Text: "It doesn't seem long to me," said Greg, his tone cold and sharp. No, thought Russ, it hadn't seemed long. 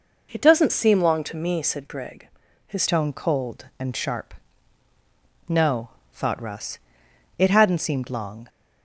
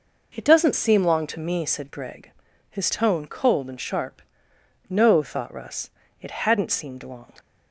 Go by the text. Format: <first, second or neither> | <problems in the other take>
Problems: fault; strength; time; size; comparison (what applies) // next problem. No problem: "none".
second | changes voice at "tone"; from 2.8 s on; 5.6 s long